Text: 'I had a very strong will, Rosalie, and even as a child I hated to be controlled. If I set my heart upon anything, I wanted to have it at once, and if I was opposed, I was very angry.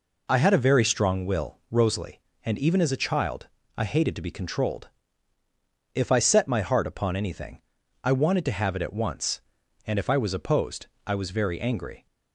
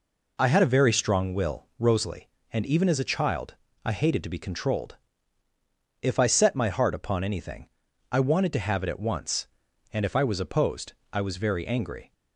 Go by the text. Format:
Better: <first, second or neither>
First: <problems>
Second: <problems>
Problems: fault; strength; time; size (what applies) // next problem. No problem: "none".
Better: neither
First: pauses between "child" and "I"; slight; at 3.4 s; 0.28 s long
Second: pauses between "child" and "I"; slight; at 3.5 s; 0.28 s long